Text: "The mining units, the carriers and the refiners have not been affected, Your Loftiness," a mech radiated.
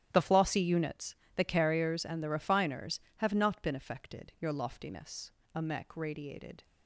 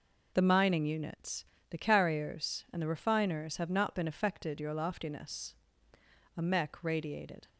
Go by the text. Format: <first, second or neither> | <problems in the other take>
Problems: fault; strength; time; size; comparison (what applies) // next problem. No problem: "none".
second | starts louder than the rest; strong; until 1.1 s; 11.5 dB // says "flossy" for "mining"; at 0.2 s